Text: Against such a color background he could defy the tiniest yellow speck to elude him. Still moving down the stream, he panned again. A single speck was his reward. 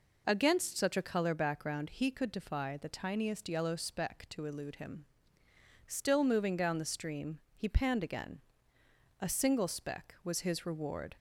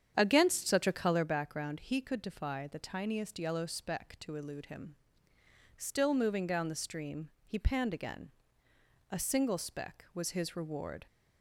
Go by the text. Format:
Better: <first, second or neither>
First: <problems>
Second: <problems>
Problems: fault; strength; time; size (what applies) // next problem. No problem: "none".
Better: first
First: none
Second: starts louder than the rest; strong; until 1.4 s; 8.5 dB